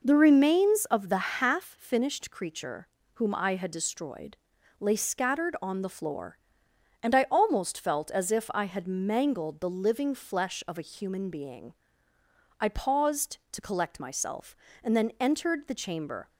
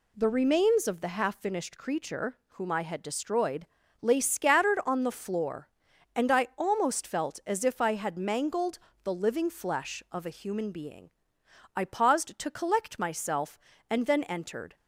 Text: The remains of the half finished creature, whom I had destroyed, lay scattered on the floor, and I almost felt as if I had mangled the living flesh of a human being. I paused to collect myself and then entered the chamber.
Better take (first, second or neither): first